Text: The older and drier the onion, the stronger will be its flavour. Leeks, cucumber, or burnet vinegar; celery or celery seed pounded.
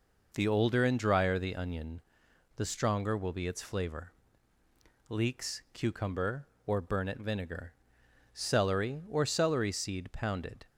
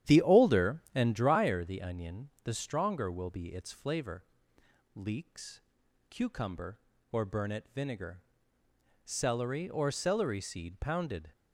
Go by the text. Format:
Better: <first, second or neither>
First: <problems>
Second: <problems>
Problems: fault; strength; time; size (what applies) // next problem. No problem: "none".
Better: first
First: none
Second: starts louder than the rest; strong; until 1.3 s; 11 dB